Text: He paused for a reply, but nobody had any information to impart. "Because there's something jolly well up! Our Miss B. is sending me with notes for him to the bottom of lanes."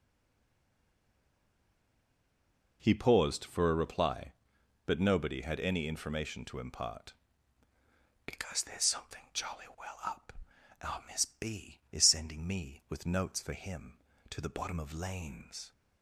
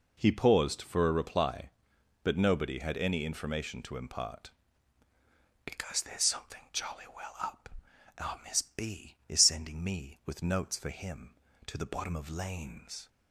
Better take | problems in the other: second | stays silent before the first word; strong; until 2.8 s; 2.8 s long

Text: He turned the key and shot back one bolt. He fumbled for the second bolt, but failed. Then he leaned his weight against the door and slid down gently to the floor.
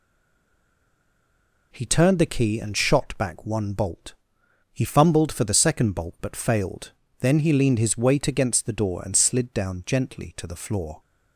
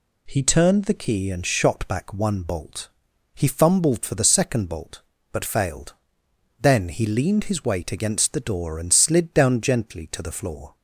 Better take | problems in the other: second | stays silent before the first word; noticeable; until 1.7 s; 1.7 s long

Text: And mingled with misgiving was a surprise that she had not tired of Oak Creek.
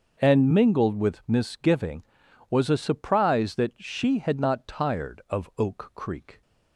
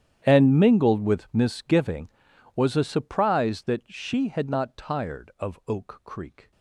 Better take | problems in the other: first | gets quieter; strong; throughout; 22 dB // starts louder than the rest; strong; until 1.2 s; 10 dB; also in the first

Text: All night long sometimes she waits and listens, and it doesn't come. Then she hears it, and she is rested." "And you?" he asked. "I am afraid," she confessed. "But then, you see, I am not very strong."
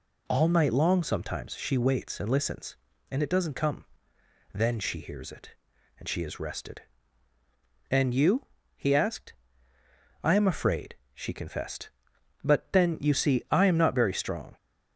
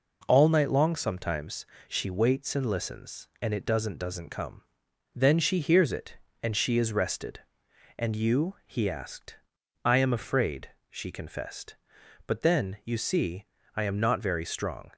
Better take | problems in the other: first | pauses between "sometimes" and "she"; slight; at 1.6 s; 0.22 s long // says "doesn't" twice; at 3.9 s

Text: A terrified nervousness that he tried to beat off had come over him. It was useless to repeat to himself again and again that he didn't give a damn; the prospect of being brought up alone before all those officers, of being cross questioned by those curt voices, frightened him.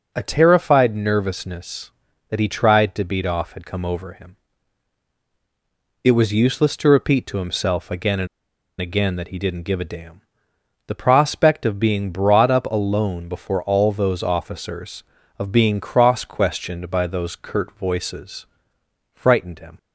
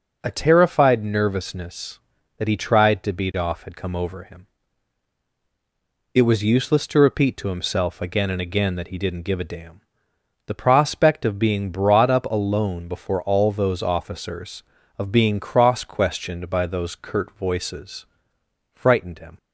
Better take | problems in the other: second | pauses between "and" and "again"; noticeable; at 8.2 s; 0.54 s long

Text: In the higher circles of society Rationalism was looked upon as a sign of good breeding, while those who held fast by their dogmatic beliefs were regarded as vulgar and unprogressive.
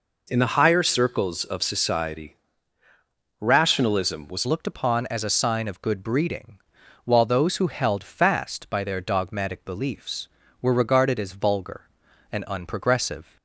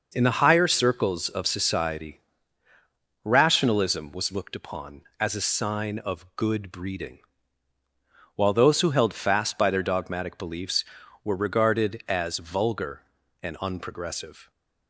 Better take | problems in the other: second | pauses between "society" and "Rationalism"; at 2.3 s; 1.0 s long; also in the second // changes voice at "looked"; from 4.4 s on; 8.9 s long

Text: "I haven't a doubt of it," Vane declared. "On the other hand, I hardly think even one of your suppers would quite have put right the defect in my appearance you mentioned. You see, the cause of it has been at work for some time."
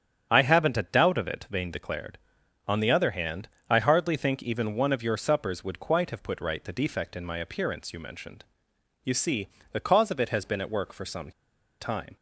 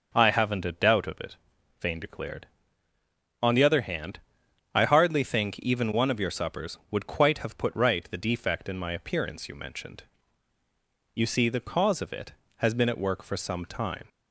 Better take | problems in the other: second | starts louder than the rest; strong; until 1.3 s; 9 dB; also in the second // pauses between "some" and "time"; noticeable; at 11.3 s; 0.50 s long

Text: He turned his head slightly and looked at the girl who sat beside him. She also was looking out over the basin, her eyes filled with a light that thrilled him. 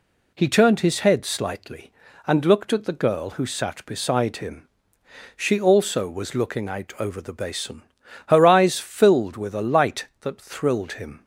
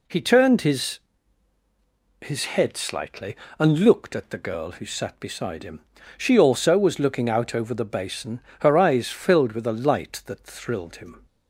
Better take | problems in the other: first | says "his" twice; at 2.2 s

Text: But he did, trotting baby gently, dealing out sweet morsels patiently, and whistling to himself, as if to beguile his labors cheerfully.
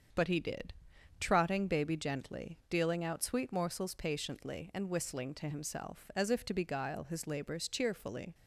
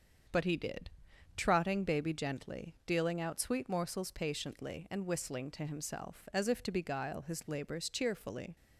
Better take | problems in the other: neither | starts louder than the rest; the same in both

